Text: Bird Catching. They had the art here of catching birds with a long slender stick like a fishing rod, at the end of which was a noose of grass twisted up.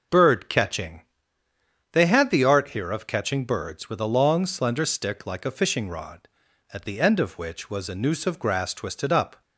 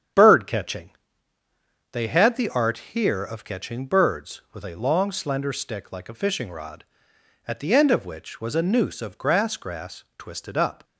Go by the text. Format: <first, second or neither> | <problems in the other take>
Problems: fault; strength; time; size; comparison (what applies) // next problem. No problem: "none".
first | starts louder than the rest; strong; until 2.1 s; 8.5 dB // pauses between "art" and "here"; slight; at 2.7 s; 0.16 s long // says "grass" twice; at 9.5 s